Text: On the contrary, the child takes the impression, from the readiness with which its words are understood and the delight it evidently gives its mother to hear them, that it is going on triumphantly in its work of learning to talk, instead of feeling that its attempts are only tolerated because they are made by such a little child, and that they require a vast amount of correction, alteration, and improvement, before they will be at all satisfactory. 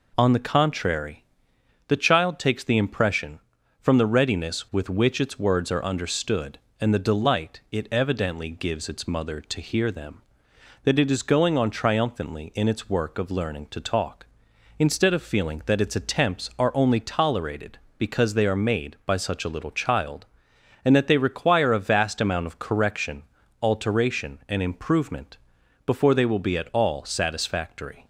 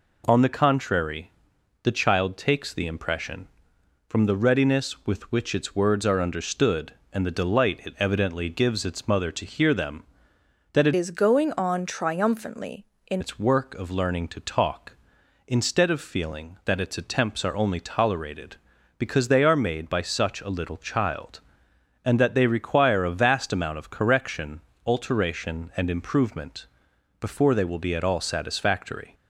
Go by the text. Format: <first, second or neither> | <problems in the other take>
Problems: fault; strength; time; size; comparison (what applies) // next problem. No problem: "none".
first | changes voice from "is" to "in"; from 10.9 to 13.2 s; 2.3 s long